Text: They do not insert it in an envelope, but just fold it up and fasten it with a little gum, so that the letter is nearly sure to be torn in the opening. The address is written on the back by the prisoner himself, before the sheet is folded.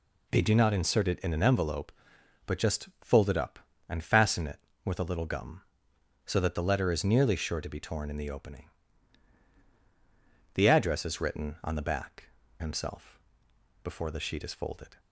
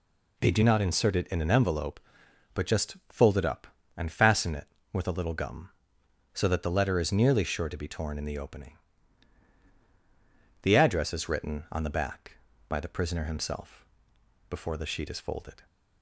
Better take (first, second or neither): second